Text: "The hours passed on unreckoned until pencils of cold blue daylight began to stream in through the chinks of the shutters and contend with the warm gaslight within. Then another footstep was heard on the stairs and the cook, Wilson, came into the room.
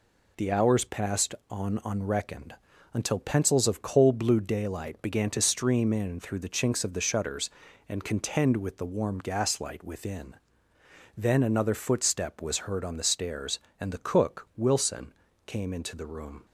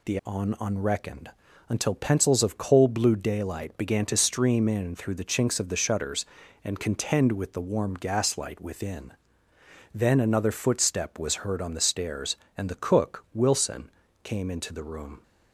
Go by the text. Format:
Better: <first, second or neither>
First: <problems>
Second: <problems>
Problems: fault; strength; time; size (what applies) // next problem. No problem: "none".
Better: first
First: pauses between "unreckoned" and "until"; at 2.5 s; 0.40 s long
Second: skips "hours passed"; at 0.2 s // pauses between "unreckoned" and "until"; at 1.3 s; 0.40 s long